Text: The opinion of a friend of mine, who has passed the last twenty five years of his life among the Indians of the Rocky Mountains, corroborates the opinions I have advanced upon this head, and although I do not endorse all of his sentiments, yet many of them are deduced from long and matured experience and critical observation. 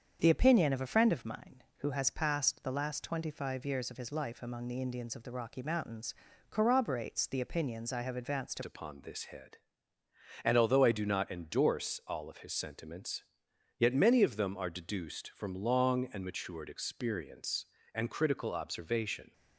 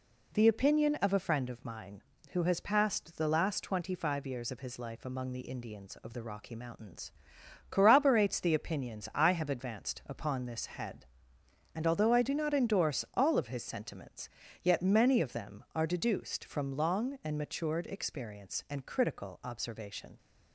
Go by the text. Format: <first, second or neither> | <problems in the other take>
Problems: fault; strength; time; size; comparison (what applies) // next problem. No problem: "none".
second | starts louder than the rest; strong; until 1.2 s; 7 dB // changes voice at "upon"; from 8.6 s on; 10.7 s long